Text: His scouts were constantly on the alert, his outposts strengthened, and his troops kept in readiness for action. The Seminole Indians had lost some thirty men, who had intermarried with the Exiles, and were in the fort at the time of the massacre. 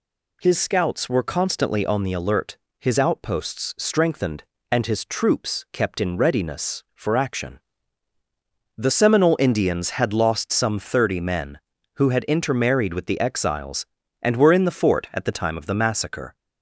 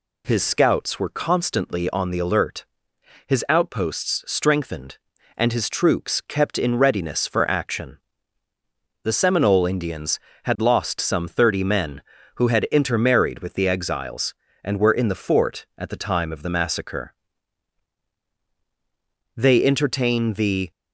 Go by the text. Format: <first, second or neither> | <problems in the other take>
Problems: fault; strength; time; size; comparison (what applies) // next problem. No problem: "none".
first | goes on to say "They entertain the"; from 19.3 s on; 1.3 s long